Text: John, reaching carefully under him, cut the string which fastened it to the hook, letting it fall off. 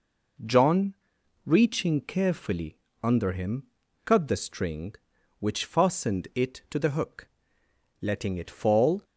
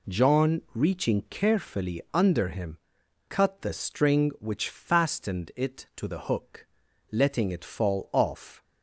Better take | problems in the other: second | pauses between "carefully" and "under"; slight; at 2.7 s; 0.24 s long // stops before "off"; at 9.0 s

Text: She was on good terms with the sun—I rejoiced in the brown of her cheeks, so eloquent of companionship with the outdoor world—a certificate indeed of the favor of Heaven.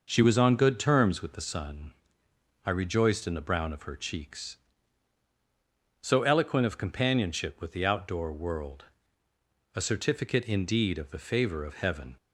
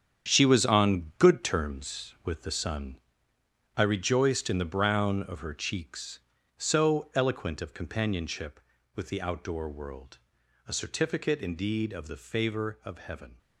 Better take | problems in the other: first | gets quieter; strong; throughout; 10.5 dB

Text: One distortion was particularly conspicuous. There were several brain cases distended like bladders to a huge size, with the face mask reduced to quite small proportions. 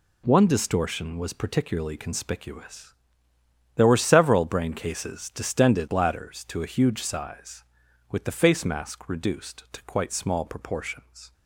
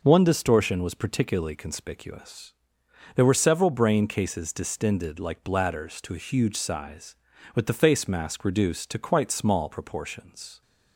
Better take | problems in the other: second | skips "like"; at 5.8 s

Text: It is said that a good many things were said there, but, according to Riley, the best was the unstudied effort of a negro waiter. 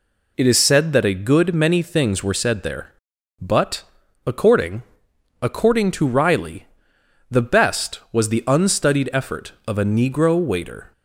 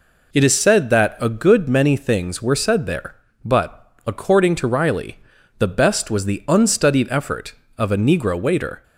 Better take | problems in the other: second | says "according" twice; at 5.4 s

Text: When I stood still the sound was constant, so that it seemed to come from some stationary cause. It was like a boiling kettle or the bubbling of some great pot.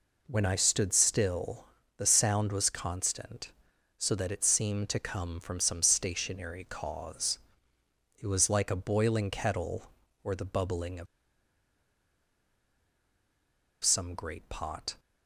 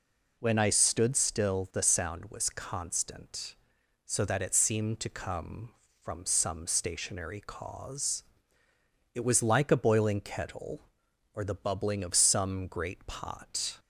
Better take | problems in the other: second | pauses between "still" and "the"; slight; at 1.6 s; 0.32 s long // pauses between "of" and "some"; strong; at 11.0 s; 2.7 s long

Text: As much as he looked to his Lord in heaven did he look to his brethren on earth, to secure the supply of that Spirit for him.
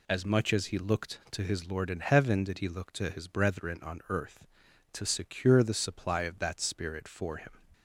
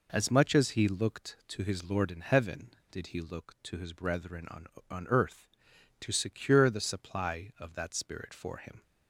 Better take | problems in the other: first | says "on" twice; at 4.8 s

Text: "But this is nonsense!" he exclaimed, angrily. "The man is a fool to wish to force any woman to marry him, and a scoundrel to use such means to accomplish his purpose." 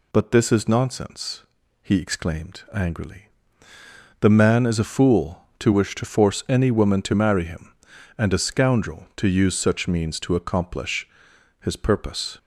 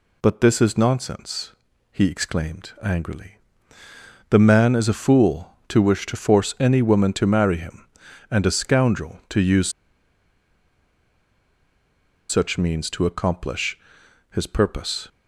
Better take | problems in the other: first | pauses between "use" and "such"; strong; at 9.7 s; 2.5 s long // pauses between "accomplish" and "his"; noticeable; at 13.7 s; 0.54 s long; noticeable in the first

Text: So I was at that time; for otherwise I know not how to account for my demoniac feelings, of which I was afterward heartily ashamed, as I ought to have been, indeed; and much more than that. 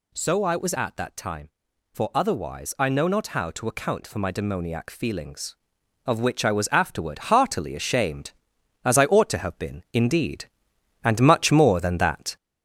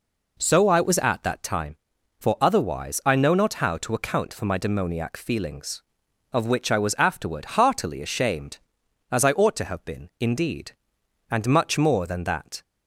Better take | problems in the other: second | gets louder; slight; throughout; 3 dB

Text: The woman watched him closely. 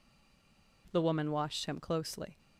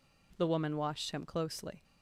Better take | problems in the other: second | stays silent before the first word; slight; until 0.8 s; 0.8 s long

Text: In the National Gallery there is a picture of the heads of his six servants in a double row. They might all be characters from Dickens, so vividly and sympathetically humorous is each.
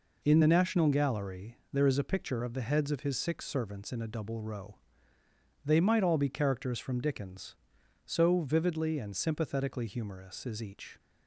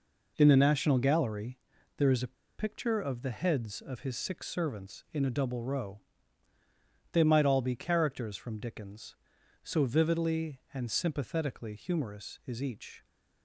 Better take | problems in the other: first | pauses between "Gallery" and "there"; at 1.5 s; 0.38 s long; slight in the first // pauses between "a" and "picture"; slight; at 2.3 s; 0.24 s long

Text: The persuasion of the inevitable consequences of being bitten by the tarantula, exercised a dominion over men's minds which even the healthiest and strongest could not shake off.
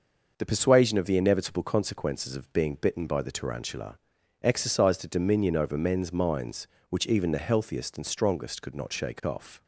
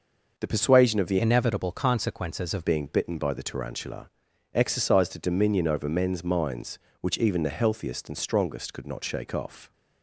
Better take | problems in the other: first | changes voice from "inevitable" to "of"; from 1.1 to 2.6 s; 1.5 s long

